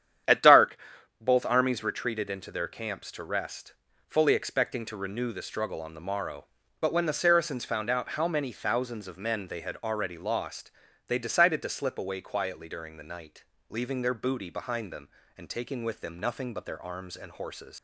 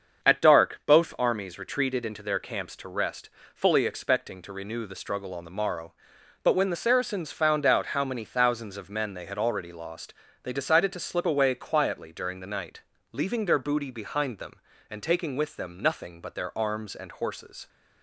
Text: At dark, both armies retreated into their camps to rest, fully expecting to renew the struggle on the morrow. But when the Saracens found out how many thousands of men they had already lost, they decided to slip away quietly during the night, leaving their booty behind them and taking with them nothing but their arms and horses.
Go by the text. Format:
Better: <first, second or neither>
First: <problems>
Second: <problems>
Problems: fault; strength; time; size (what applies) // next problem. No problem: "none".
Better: second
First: starts louder than the rest; strong; until 1.7 s; 9.5 dB // leaves "horses" unfinished; at 17.7 s; 110 ms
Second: starts louder than the rest; until 1.3 s; 7 dB